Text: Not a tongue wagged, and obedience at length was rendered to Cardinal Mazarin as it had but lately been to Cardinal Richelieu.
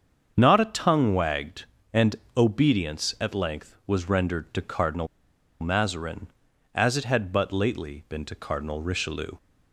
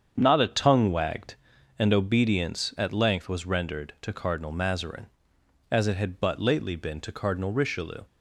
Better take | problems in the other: second | starts louder than the rest; strong; until 1.3 s; 7.5 dB; strong in the second // pauses between "and" and "obedience"; slight; at 2.1 s; 0.20 s long // pauses between "Cardinal" and "Mazarin"; noticeable; at 5.0 s; 0.54 s long

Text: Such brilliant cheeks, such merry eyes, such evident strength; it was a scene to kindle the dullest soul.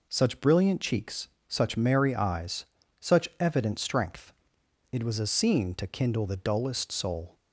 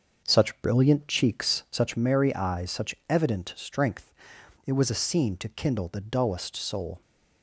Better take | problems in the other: first | starts louder than the rest; until 2.0 s; 6.5 dB

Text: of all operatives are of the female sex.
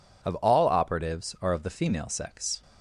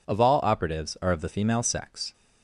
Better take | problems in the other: neither | none

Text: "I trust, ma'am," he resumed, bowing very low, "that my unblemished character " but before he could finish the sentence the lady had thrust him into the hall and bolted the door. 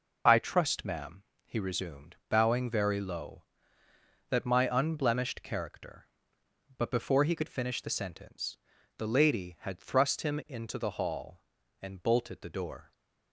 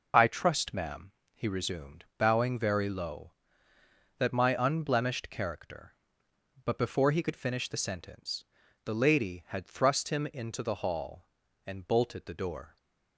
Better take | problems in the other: neither | pauses between "sentence" and "the"; the same in both

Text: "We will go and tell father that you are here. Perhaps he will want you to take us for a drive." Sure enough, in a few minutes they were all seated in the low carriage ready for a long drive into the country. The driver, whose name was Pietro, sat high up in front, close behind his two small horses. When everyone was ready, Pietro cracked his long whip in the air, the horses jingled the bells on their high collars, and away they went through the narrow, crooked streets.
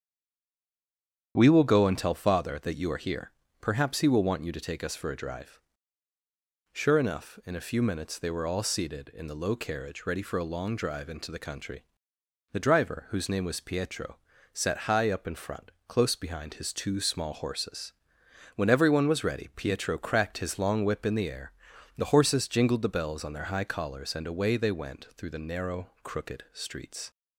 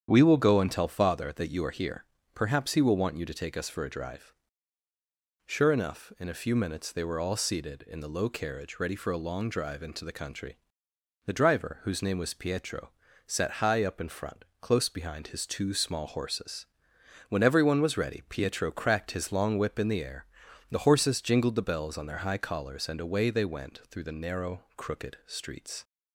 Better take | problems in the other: second | stays silent before the first word; noticeable; until 1.3 s; 1.3 s long // starts louder than the rest; strong; until 2.3 s; 8.5 dB; strong in the second

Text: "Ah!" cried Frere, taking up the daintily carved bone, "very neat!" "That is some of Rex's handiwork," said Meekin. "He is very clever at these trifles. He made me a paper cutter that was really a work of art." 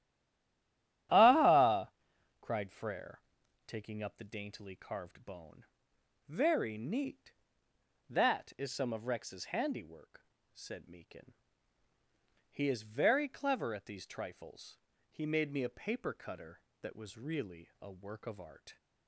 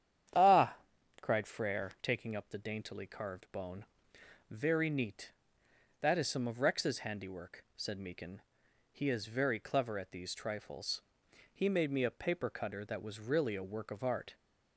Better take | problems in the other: second | stays silent before the first word; until 1.0 s; 1.0 s long // starts louder than the rest; strong; until 2.6 s; 12.5 dB; strong in the second

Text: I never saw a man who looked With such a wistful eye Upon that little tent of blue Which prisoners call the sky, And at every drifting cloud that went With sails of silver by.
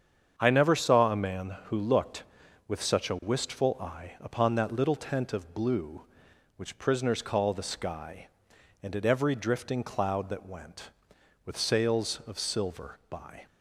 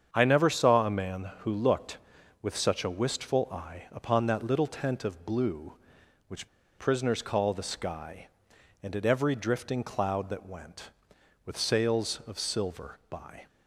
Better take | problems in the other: first | starts louder than the rest; strong; until 1.1 s; 7.5 dB; strong in the first // pauses between "Which" and "prisoners"; slight; at 6.4 s; 0.29 s long

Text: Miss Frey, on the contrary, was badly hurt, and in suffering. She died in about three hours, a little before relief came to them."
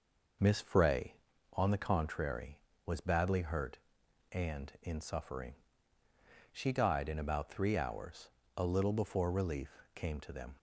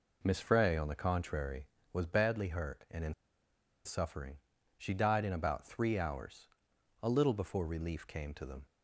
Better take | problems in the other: first | pauses between "in" and "suffering"; noticeable; at 3.1 s; 0.73 s long

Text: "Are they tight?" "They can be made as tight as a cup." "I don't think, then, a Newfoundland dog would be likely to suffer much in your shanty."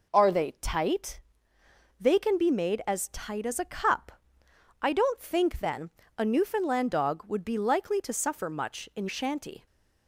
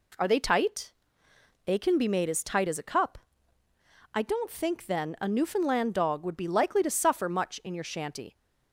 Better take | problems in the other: second | skips "your"; at 9.0 s

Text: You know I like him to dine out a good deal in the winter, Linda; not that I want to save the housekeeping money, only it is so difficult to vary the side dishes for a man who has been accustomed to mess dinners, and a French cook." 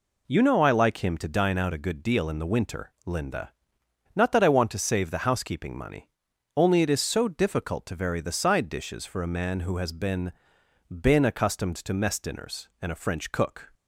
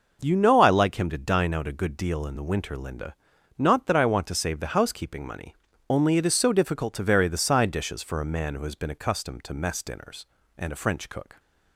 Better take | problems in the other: second | says "been" twice; at 10.8 s

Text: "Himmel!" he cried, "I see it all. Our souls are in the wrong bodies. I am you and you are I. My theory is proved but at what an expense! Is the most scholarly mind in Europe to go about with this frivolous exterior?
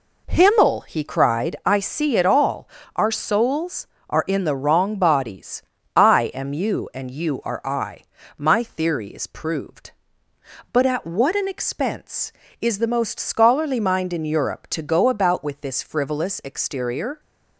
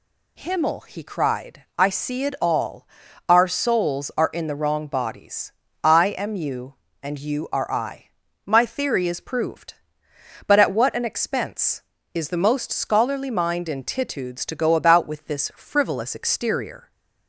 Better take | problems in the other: first | says "Titudes" for "Europe"; at 13.8 s

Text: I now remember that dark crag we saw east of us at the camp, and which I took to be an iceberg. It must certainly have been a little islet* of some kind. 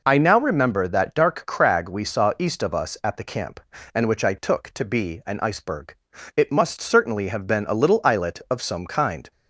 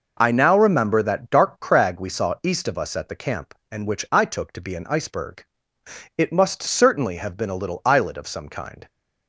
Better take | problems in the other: neither | none

